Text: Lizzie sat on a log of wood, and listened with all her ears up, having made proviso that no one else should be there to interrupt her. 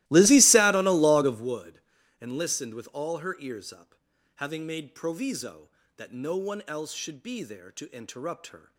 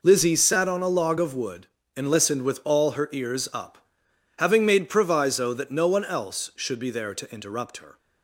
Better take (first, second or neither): second